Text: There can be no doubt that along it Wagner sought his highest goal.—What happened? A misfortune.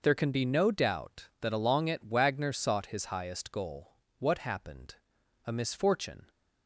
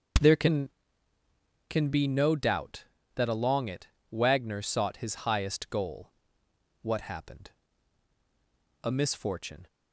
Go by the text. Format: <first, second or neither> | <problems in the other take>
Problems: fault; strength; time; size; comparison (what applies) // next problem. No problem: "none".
first | says "can" twice; at 1.6 s // pauses between "it" and "Wagner"; slight; at 3.8 s; 0.22 s long